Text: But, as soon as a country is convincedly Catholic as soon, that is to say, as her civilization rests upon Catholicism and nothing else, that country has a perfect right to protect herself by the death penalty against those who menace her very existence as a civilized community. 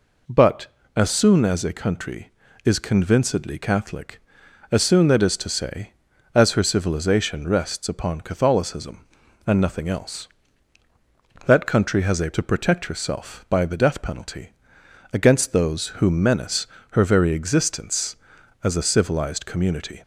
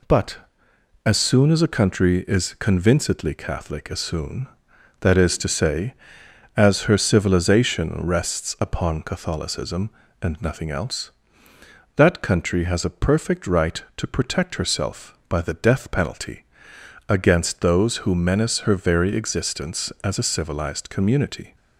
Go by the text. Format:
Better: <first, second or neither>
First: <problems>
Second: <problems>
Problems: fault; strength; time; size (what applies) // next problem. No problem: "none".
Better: second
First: skips "perfect right"; at 12.3 s // pauses between "penalty" and "against"; noticeable; at 14.5 s; 0.62 s long // pauses between "menace" and "her"; slight; at 16.6 s; 0.24 s long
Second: pauses between "penalty" and "against"; noticeable; at 16.4 s; 0.64 s long